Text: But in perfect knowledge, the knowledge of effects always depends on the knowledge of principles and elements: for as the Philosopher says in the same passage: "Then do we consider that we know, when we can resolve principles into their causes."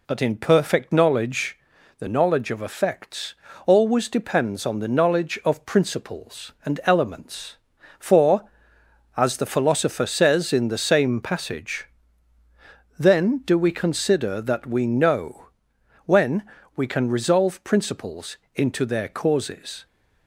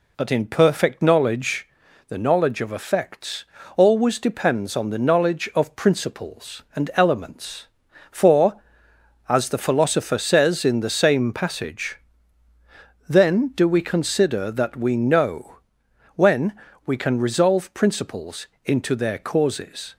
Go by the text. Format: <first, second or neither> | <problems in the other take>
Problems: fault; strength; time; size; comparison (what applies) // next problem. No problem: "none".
neither | pauses between "effects" and "always"; slight; the same in both // pauses between "when" and "we"; slight; the same in both // pauses between "principles" and "into"; slight; the same in both